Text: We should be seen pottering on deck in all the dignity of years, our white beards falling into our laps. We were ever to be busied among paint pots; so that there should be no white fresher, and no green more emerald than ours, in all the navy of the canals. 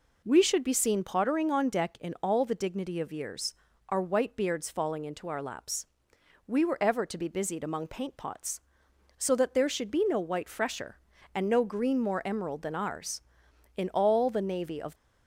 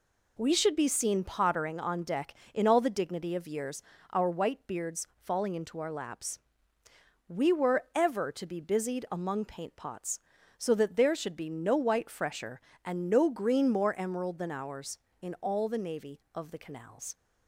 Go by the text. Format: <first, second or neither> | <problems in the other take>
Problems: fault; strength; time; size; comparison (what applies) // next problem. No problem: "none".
second | stops before "the canals"; at 14.9 s